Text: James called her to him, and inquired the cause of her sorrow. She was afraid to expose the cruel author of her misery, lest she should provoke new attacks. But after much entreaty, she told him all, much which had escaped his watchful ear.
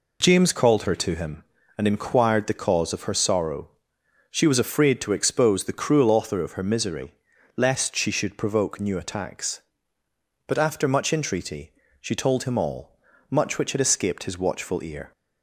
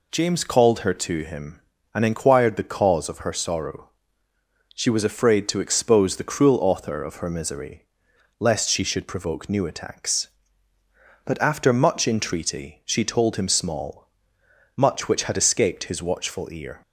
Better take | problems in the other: first | says "small" for "all"; at 13.4 s

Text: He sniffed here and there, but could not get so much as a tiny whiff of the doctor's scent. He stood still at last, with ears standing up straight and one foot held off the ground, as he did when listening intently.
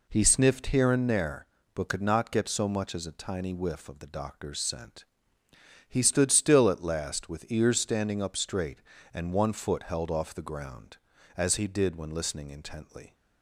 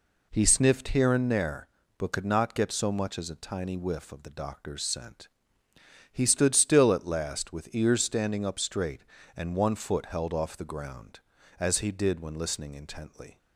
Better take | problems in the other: neither | none

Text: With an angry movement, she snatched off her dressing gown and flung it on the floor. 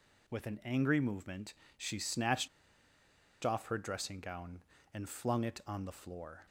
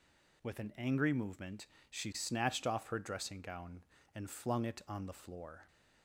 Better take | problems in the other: second | pauses between "snatched" and "off"; noticeable; at 2.4 s; 0.95 s long

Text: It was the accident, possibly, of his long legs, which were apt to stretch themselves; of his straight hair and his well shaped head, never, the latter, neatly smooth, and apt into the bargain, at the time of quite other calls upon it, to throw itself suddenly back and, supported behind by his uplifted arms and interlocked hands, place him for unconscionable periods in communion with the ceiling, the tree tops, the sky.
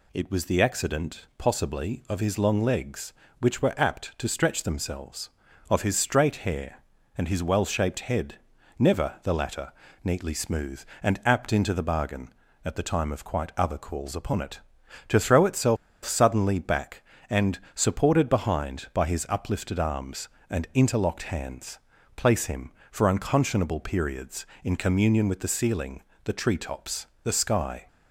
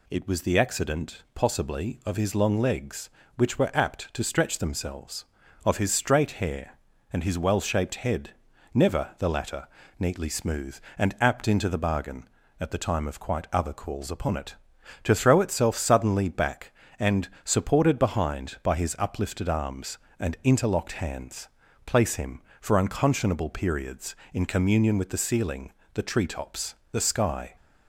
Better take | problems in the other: second | pauses between "itself" and "suddenly"; slight; at 15.7 s; 0.28 s long

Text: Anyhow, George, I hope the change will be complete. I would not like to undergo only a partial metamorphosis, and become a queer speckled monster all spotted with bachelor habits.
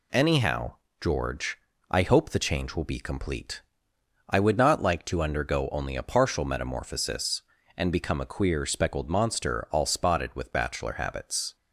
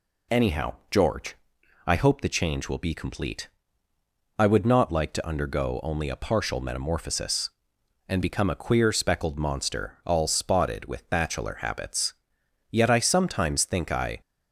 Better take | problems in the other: first | goes on to say "Yet I sometimes think I"; from 12.7 s on; 1.5 s long

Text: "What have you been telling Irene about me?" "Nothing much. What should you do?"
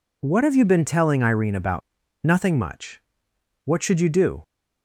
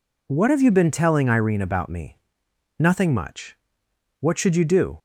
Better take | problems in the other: second | skips "me"; at 2.0 s

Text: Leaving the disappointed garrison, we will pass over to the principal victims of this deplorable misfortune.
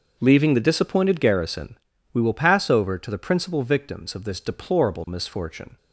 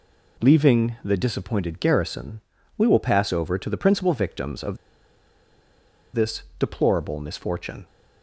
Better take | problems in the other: first | pauses between "of" and "this"; strong; at 4.7 s; 1.3 s long

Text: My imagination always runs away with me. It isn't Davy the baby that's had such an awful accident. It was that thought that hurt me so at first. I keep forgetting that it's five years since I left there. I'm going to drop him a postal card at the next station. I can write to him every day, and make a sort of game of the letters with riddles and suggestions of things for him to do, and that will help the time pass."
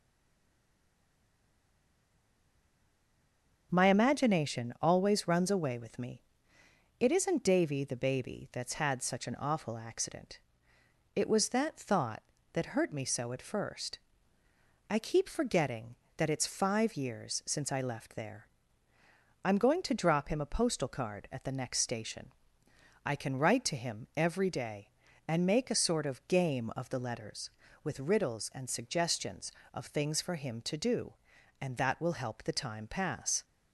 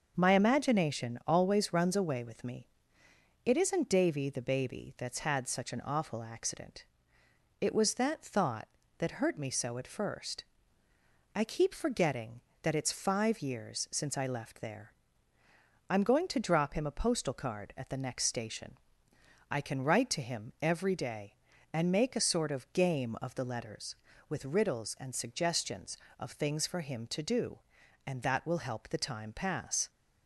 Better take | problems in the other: second | stays silent before the first word; strong; until 3.7 s; 3.7 s long // starts louder than the rest; noticeable; until 4.7 s; 6 dB; noticeable in the second

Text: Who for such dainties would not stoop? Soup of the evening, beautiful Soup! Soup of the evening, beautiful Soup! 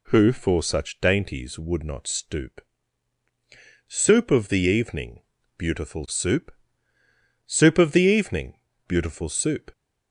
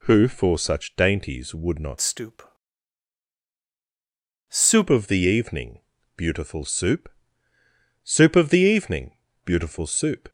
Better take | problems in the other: first | changes voice from "stoop" to "Soup"; from 2.0 to 4.8 s; 2.8 s long

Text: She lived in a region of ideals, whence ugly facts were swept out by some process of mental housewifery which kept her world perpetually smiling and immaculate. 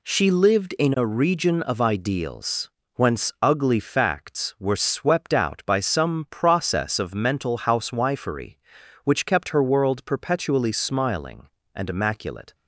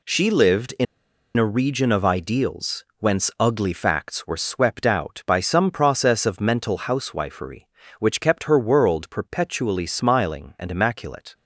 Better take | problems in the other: first | pauses between "in" and "a"; noticeable; at 0.8 s; 0.52 s long

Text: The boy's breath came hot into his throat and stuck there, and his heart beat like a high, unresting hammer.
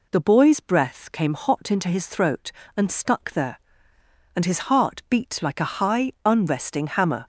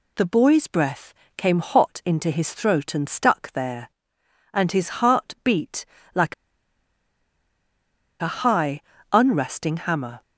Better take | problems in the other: first | pauses between "breath" and "came"; slight; at 1.1 s; 0.24 s long // pauses between "beat" and "like"; slight; at 5.8 s; 0.28 s long // pauses between "like" and "a"; strong; at 6.3 s; 1.8 s long

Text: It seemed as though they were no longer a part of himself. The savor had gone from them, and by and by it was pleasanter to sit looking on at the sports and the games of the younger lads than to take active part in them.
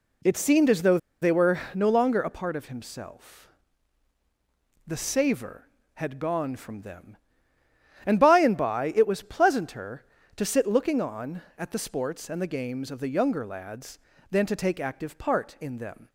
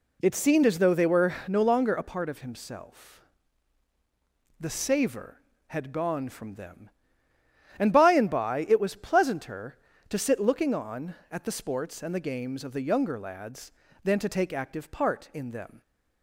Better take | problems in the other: second | pauses between "though" and "they"; slight; at 0.9 s; 0.24 s long

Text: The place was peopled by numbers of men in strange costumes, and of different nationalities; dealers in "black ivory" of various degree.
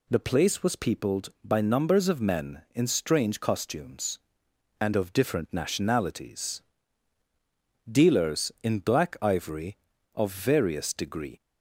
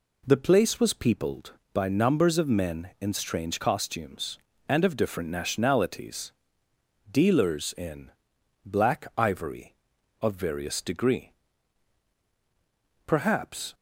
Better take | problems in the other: first | pauses between "in" and "black"; noticeable; at 8.0 s; 0.54 s long // goes on to say "Perhaps"; noticeable; from 13.0 s on; 0.68 s long

